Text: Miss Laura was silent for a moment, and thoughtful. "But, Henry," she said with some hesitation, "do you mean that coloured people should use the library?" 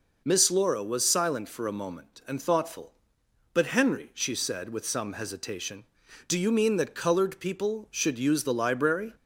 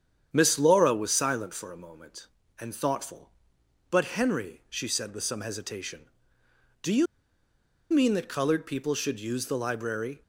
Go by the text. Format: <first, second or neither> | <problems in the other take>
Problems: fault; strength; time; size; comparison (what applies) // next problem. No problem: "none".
first | starts louder than the rest; strong; until 1.3 s; 8.5 dB // pauses between "you" and "mean"; noticeable; at 7.0 s; 0.85 s long